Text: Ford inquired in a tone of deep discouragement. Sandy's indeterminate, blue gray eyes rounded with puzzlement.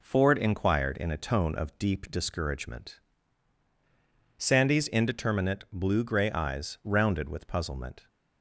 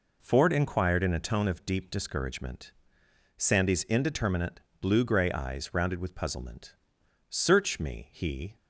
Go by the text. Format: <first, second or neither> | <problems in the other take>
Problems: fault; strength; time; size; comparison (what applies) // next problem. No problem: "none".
first | goes on to say "Search me he"; noticeable; from 7.2 s on; 1.2 s long